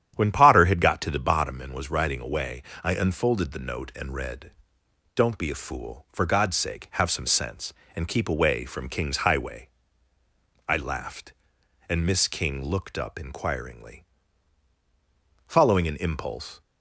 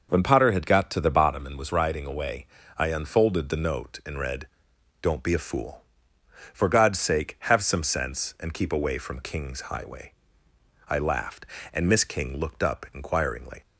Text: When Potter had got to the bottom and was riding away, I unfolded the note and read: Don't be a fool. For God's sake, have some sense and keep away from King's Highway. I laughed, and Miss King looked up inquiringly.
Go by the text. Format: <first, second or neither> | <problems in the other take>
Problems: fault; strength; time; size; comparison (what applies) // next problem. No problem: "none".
second | starts louder than the rest; strong; until 1.1 s; 9.5 dB // goes on to say "Following an impulse"; noticeable; from 15.4 s on; 1.1 s long